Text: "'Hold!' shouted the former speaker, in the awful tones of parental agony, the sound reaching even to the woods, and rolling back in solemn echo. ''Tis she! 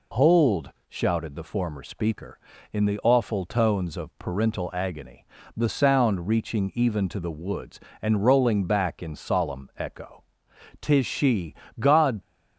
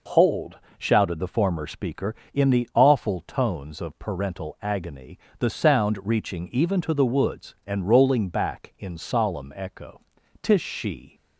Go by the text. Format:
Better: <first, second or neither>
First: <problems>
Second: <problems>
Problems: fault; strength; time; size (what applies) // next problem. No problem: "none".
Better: second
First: goes on to say "God"; slight; from 11.8 s on; 0.40 s long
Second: none